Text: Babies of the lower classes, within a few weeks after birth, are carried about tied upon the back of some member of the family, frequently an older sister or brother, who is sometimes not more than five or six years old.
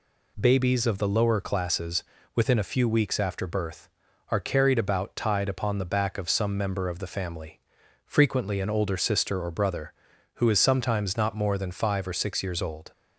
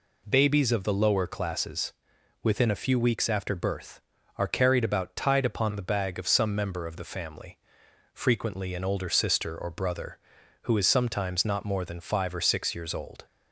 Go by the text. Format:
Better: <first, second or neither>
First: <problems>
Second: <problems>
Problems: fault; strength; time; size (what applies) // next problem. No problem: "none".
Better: first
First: none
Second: says "bag" for "back"; at 5.8 s